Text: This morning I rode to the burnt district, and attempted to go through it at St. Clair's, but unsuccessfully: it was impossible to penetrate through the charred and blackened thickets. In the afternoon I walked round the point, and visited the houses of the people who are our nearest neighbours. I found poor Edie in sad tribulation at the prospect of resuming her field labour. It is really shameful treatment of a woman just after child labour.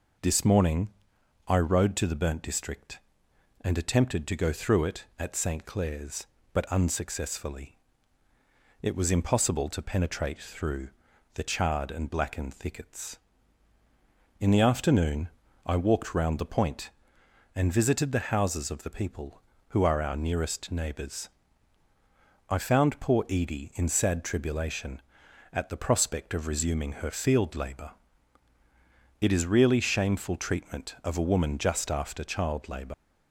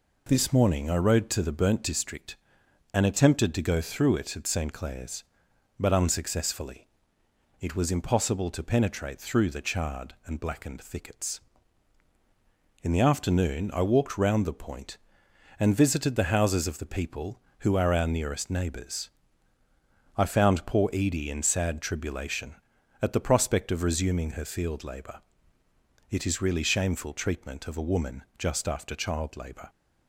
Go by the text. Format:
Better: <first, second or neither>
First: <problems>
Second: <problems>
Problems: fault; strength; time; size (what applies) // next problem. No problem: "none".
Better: second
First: pauses between "morning" and "I"; noticeable; at 0.8 s; 0.58 s long // pauses between "through" and "the"; noticeable; at 10.8 s; 0.46 s long // pauses between "afternoon" and "I"; slight; at 15.2 s; 0.36 s long // leaves "labour" unfinished; at 32.9 s; 135 ms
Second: none